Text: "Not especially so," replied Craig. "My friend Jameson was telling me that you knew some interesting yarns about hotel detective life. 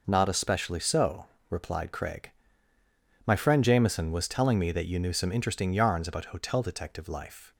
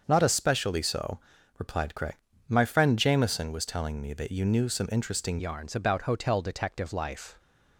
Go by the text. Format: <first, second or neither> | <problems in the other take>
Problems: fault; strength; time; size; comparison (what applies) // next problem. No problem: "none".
first | starts louder than the rest; until 1.0 s; 6.5 dB // changes voice at "yarns"; from 5.3 s on; 2.0 s long